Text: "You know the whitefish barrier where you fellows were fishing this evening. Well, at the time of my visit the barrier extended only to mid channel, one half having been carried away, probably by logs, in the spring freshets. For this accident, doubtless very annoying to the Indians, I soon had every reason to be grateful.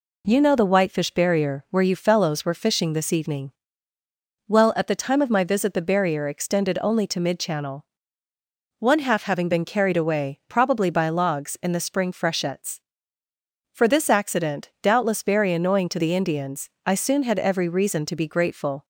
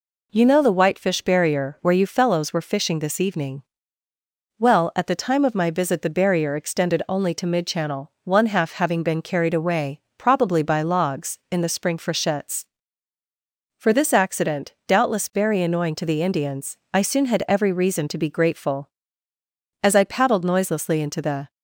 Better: first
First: none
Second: goes on to say "As I paddled noiselessly into the"; strong; from 19.8 s on; 1.6 s long

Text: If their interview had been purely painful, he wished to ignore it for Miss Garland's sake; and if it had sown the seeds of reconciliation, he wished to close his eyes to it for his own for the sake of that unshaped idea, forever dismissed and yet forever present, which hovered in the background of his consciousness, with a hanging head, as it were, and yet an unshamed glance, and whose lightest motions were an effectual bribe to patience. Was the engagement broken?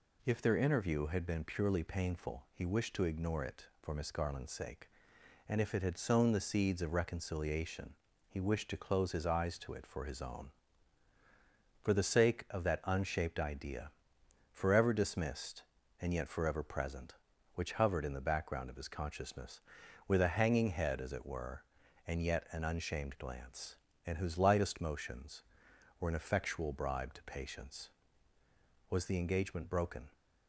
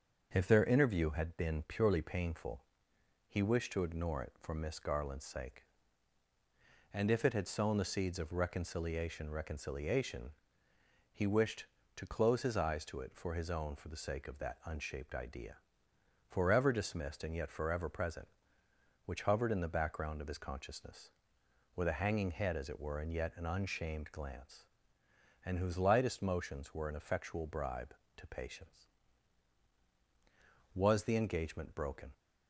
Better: first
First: none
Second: starts louder than the rest; until 1.3 s; 6.5 dB // says "reconciliation" twice; at 9.2 s

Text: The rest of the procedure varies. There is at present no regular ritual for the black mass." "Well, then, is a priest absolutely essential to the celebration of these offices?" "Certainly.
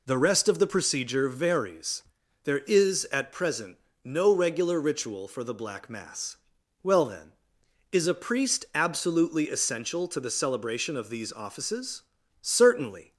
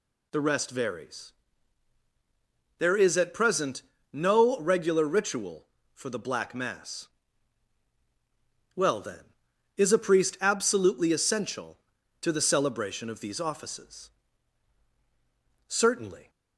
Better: first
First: pauses between "present" and "no"; slight; at 3.7 s; 0.26 s long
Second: skips "of the procedure"; at 0.6 s // pauses between "present" and "no"; slight; at 3.8 s; 0.32 s long

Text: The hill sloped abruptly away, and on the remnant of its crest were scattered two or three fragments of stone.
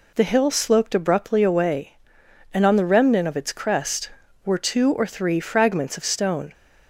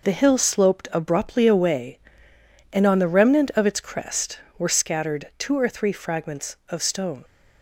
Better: second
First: skips "scattered"; at 4.5 s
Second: none

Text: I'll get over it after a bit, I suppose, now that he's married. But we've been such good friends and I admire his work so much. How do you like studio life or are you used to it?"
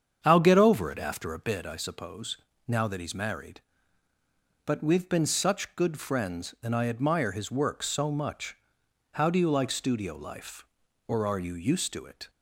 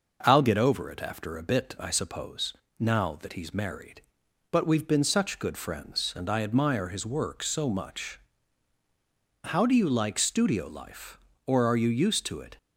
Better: second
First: starts louder than the rest; strong; until 1.4 s; 7.5 dB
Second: none

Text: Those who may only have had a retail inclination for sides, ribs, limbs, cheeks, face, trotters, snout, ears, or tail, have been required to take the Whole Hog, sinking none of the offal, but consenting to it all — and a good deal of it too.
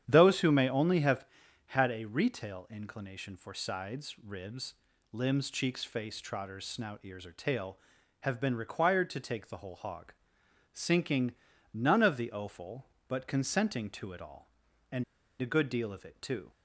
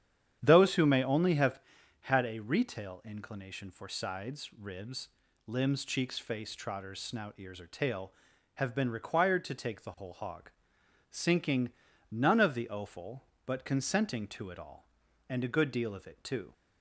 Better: second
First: starts louder than the rest; strong; until 1.0 s; 9.5 dB // pauses between "sinking" and "none"; at 11.3 s; 0.40 s long // pauses between "and" and "a"; at 15.0 s; 0.38 s long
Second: starts louder than the rest; strong; until 1.4 s; 9.5 dB // pauses between "sinking" and "none"; at 11.7 s; 0.40 s long

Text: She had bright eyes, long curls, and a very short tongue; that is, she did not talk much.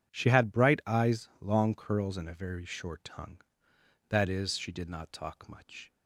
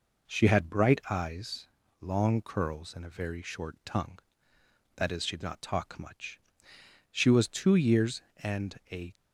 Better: first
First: none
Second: goes on to say "She was two years and a"; strong; from 7.1 s on; 2.0 s long

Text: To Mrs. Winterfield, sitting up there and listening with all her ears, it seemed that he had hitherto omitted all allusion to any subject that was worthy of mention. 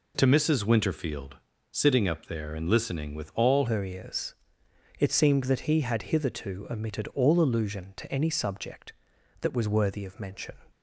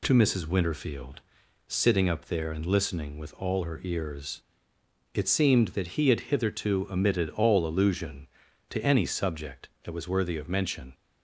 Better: second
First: changes voice at "her"; from 3.6 s on; 6.9 s long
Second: none

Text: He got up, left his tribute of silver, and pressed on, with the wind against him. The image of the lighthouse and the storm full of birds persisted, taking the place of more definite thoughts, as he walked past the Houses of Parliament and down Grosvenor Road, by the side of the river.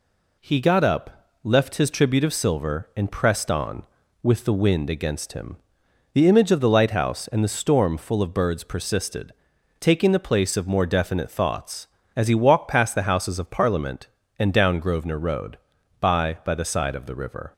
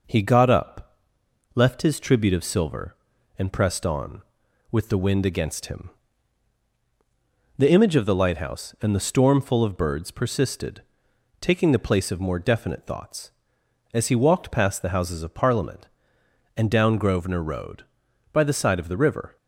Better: second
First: says "by" twice; at 16.4 s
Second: none

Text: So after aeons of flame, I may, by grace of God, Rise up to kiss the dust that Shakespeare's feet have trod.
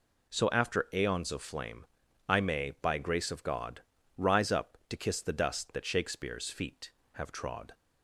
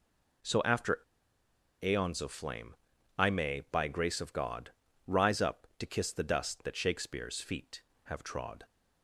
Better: first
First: none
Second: pauses between "after" and "aeons"; noticeable; at 0.9 s; 0.84 s long

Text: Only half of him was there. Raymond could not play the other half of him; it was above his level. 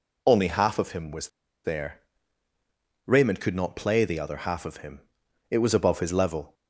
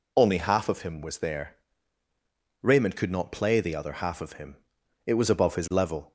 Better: second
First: pauses between "was" and "there"; slight; at 1.2 s; 0.35 s long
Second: none

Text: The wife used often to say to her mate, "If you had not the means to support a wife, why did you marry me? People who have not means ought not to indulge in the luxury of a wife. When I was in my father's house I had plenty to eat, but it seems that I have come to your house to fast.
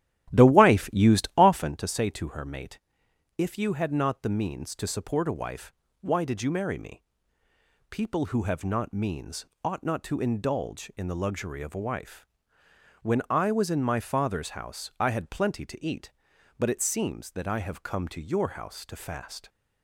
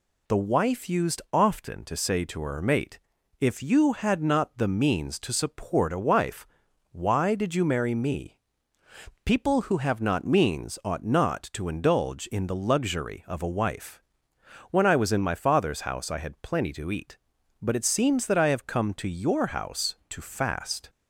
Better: second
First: starts louder than the rest; strong; until 1.9 s; 13.5 dB // pauses between "means" and "ought"; slight; at 9.4 s; 0.18 s long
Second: none

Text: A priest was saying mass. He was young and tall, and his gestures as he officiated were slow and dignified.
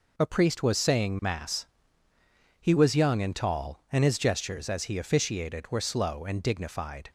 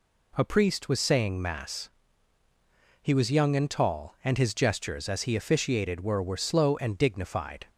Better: first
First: none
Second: says "were" twice; at 6.2 s

